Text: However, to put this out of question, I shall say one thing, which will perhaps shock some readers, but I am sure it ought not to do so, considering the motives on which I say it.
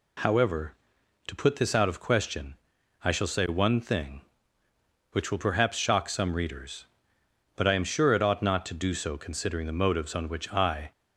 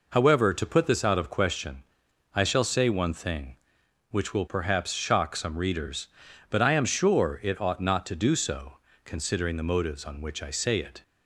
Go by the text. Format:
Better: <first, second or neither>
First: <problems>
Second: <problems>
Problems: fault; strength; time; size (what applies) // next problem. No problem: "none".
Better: second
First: stops before "say it"; at 10.9 s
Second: none